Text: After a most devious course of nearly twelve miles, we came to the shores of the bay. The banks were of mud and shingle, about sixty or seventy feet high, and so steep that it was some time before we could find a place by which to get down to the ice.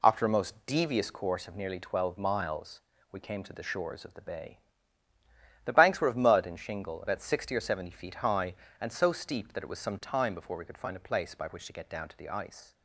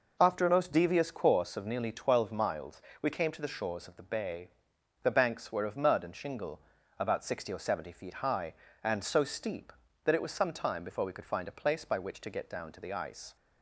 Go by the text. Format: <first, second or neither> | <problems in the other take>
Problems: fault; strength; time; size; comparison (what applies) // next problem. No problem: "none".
neither | none